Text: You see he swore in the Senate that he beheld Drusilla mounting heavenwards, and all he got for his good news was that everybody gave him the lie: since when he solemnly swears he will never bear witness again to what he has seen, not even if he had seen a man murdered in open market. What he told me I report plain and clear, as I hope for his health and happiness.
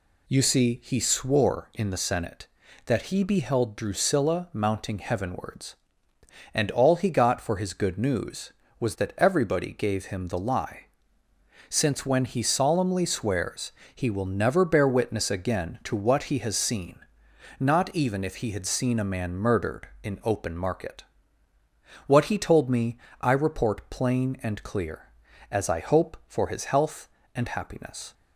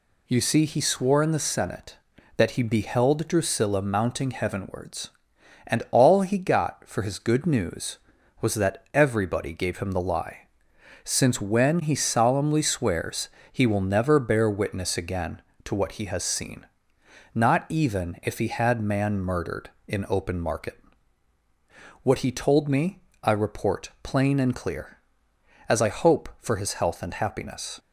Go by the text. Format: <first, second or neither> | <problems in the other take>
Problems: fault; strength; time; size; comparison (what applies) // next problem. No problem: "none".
first | pauses between "swears" and "he"; slight; at 13.2 s; 0.24 s long; slight in the first // skips "seen a"; at 18.8 s // pauses between "me" and "I"; slight; at 22.9 s; 0.24 s long; slight in the first